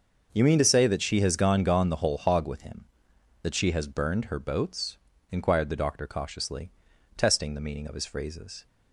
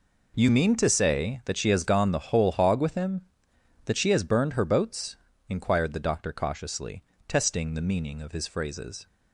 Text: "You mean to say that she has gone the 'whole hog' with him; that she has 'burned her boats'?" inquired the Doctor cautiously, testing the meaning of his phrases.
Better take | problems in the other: second | starts louder than the rest; until 1.3 s; 6.5 dB // says "gone" twice; at 1.6 s

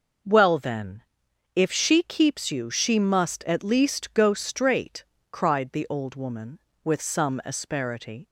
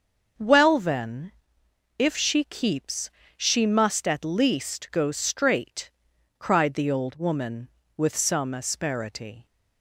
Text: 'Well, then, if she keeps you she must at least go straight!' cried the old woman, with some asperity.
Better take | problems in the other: first | starts louder than the rest; until 2.0 s; 6.5 dB // skips "you"; at 3.2 s

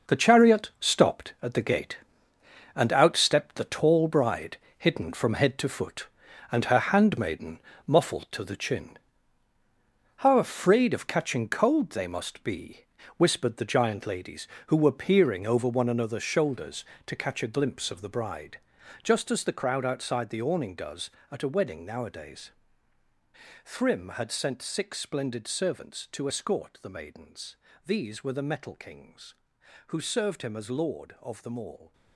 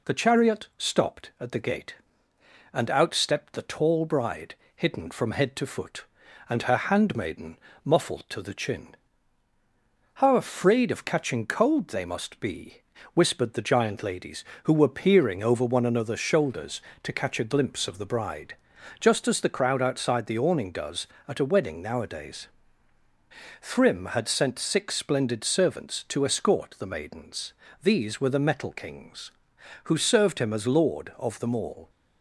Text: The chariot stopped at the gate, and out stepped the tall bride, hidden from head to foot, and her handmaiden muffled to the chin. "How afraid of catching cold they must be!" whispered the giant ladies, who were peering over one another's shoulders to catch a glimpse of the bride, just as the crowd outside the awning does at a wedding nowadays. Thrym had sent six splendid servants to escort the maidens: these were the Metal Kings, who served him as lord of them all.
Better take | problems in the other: second | gets quieter; strong; throughout; 10.5 dB // pauses between "handmaiden" and "muffled"; slight; at 7.6 s; 0.26 s long; slight in the second

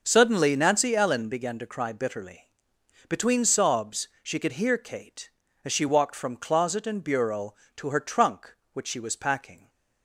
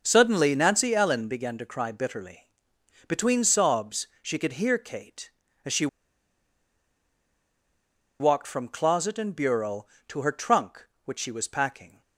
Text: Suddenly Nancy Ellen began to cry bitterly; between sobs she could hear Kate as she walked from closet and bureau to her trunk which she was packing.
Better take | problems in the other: first | pauses between "she" and "walked"; strong; at 5.8 s; 2.3 s long

